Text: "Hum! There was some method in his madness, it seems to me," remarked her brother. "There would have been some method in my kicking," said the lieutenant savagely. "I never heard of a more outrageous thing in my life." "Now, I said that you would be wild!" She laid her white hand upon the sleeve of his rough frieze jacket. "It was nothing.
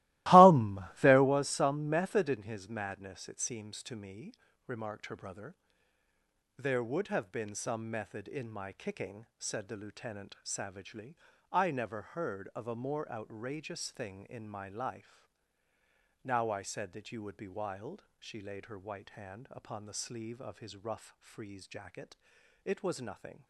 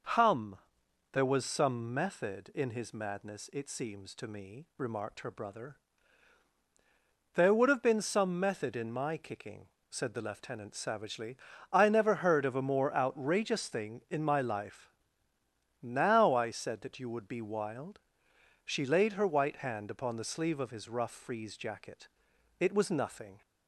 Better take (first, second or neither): second